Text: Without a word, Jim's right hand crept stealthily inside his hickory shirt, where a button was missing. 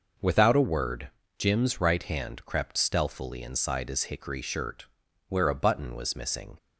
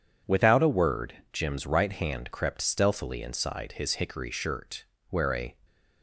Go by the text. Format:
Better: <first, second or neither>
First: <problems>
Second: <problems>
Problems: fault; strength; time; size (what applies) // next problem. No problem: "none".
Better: first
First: none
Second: stops before "button was missing"; at 5.6 s